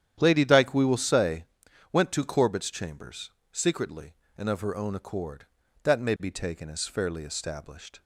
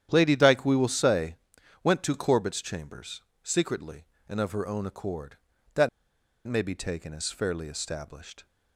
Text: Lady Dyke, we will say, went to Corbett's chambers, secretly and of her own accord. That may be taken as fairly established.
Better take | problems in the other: first | starts louder than the rest; strong; until 1.1 s; 10 dB; strong in the first // pauses between "That" and "may"; noticeable; at 5.8 s; 0.58 s long

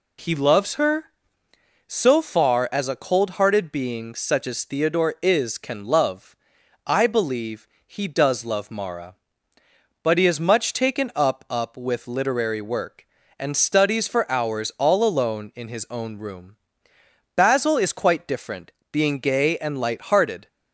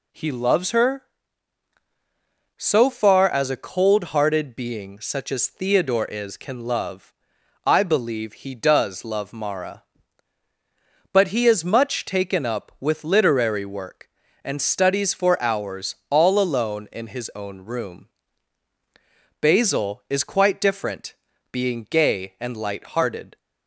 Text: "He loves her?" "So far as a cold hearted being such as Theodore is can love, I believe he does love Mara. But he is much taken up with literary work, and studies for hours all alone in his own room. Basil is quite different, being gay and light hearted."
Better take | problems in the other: second | pauses between "believe" and "he"; slight; at 7.6 s; 0.22 s long // says "up" twice; at 11.4 s

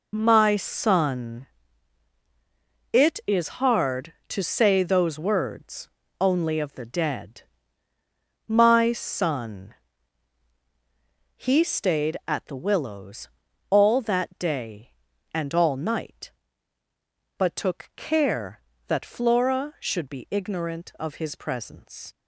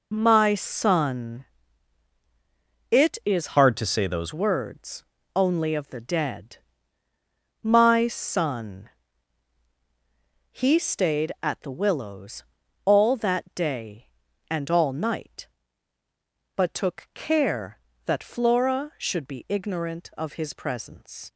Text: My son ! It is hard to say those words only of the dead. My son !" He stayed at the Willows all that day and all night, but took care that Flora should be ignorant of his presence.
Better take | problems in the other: first | changes voice from "hard" to "those"; from 3.5 to 4.3 s; 0.8 s long // pauses between "words" and "only"; slight; at 5.0 s; 0.32 s long; slight in the first // pauses between "Willows" and "all"; at 12.4 s; 0.42 s long; also in the first

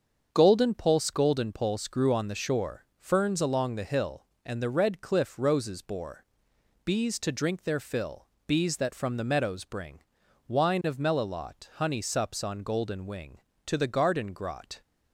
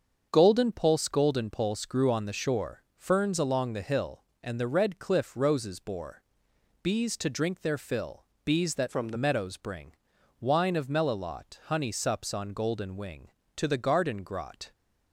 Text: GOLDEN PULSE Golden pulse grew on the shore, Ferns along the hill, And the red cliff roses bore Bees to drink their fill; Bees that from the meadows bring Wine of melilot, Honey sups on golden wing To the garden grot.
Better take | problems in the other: first | starts louder than the rest; until 1.3 s; 7 dB; also in the first // pauses between "bore" and "Bees"; noticeable; at 6.2 s; 0.62 s long; noticeable in the first // changes voice from "from" to "the"; from 8.8 to 9.1 s; 0.3 s long // pauses between "bring" and "Wine"; at 9.9 s; 0.42 s long; also in the first

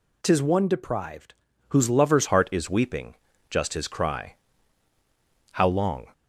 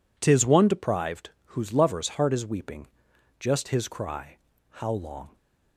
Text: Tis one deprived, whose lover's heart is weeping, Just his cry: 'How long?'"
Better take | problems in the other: second | changes voice at "heart"; from 2.2 s on; 3.8 s long

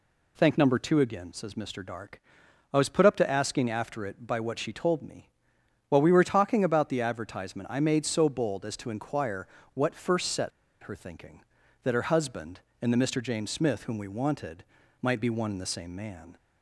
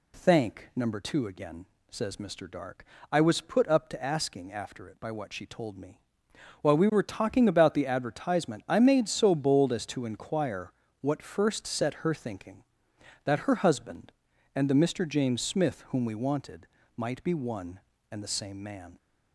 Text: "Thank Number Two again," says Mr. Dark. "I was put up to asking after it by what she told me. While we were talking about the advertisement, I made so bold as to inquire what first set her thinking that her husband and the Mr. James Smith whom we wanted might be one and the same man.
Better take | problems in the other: second | pauses between "inquire" and "what"; slight; at 9.4 s; 0.28 s long; slight in the second // pauses between "set" and "her"; slight; at 10.5 s; 0.32 s long // pauses between "wanted" and "might"; at 14.6 s; 0.40 s long; slight in the second

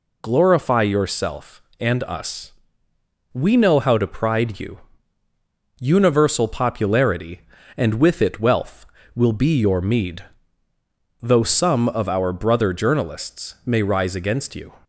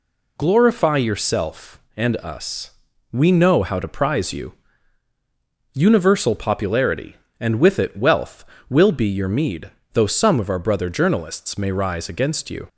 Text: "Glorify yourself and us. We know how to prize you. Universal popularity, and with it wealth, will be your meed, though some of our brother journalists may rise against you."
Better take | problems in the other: second | says "pride" for "prize"; at 4.0 s

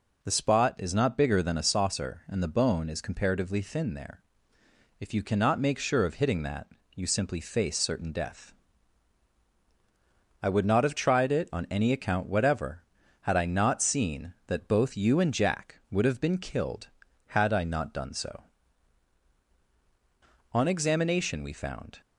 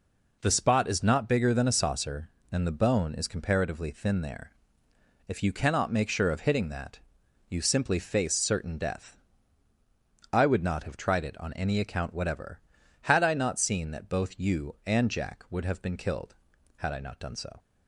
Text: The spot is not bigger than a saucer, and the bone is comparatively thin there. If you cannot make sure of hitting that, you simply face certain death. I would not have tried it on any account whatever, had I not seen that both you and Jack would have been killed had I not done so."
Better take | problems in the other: second | goes on to say "On examination we found"; from 20.5 s on; 1.4 s long

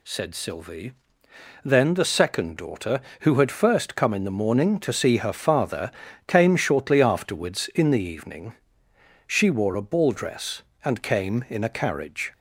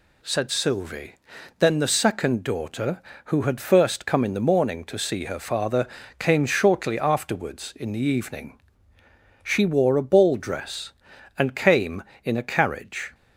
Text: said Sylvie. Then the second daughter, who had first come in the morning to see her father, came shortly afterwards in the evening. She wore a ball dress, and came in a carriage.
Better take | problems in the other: neither | none

